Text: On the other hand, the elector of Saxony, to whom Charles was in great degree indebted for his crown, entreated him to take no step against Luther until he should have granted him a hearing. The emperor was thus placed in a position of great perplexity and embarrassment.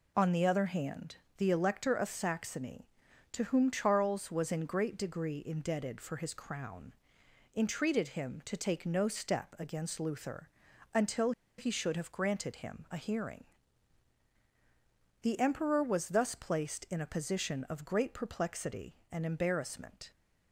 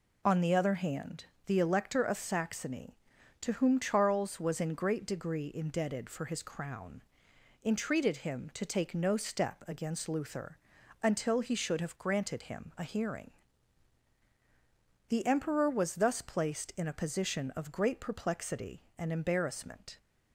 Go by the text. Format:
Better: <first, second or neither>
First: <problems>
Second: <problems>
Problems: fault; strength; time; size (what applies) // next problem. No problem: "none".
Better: second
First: pauses between "Luther" and "until"; at 10.4 s; 0.44 s long // pauses between "until" and "he"; slight; at 11.3 s; 0.27 s long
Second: pauses between "Luther" and "until"; at 10.5 s; 0.44 s long